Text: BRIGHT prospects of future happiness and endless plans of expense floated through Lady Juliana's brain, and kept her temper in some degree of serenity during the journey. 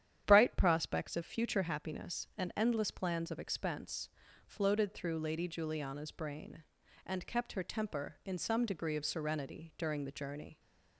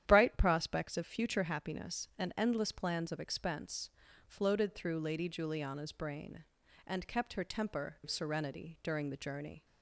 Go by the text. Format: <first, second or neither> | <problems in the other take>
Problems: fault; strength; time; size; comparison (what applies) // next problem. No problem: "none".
first | starts louder than the rest; strong; until 1.0 s; 10.5 dB; strong in the first // pauses between "expense" and "floated"; at 3.8 s; 0.38 s long; also in the first // skips "in some degree"; at 7.9 s